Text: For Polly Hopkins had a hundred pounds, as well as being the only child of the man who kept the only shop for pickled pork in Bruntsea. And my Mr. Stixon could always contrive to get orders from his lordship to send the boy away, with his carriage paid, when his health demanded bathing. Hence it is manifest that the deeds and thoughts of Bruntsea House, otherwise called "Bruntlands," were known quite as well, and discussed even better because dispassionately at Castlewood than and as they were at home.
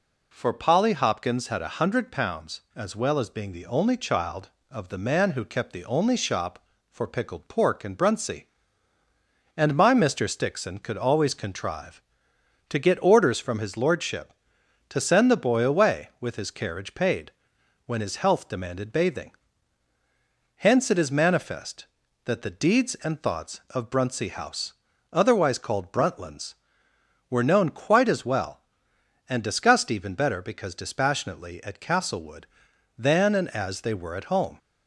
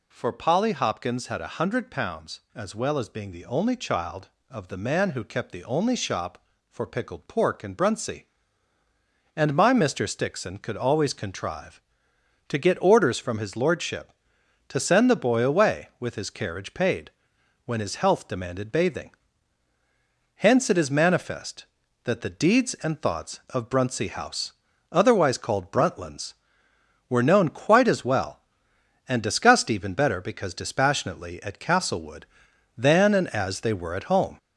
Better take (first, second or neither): first